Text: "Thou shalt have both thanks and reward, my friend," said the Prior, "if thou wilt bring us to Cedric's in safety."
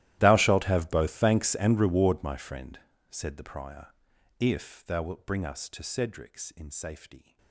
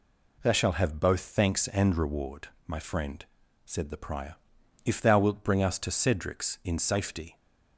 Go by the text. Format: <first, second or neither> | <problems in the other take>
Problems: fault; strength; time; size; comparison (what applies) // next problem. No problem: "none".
second | gets quieter; strong; throughout; 23.5 dB